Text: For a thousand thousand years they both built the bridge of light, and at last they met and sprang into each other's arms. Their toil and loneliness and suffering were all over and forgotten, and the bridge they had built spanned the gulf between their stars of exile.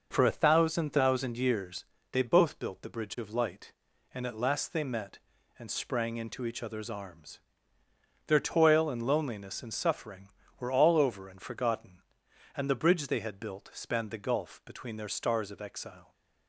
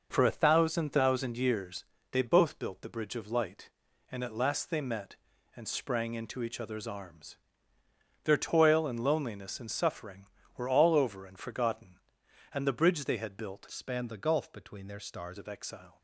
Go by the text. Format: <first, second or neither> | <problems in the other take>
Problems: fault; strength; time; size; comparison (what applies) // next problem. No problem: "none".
first | pauses between "years" and "they"; slight; at 1.8 s; 0.26 s long; slight in the first // changes voice from "spanned" to "stars"; from 13.6 to 15.3 s; 1.7 s long